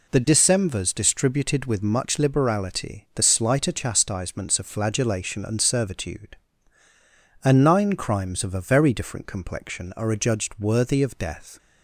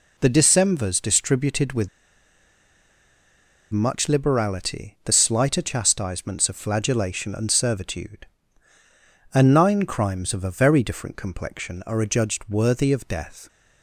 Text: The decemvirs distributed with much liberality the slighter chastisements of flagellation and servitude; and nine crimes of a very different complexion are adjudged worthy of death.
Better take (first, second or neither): first